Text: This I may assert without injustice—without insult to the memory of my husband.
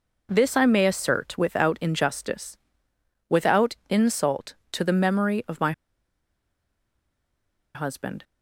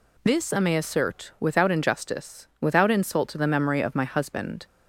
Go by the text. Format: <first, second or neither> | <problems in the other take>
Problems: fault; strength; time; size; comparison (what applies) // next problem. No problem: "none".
second | pauses between "my" and "husband"; strong; at 5.7 s; 2.0 s long